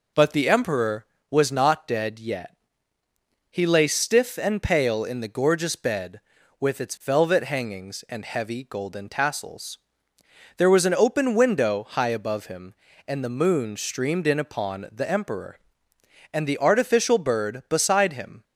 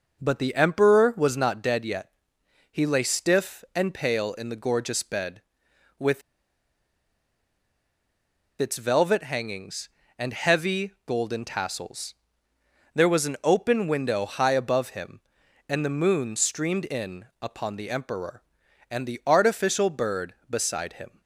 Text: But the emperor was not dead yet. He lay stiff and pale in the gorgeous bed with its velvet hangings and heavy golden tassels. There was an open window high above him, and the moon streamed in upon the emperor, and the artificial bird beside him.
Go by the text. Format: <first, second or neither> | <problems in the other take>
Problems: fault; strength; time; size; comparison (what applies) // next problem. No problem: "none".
first | pauses between "with" and "its"; strong; at 6.2 s; 2.3 s long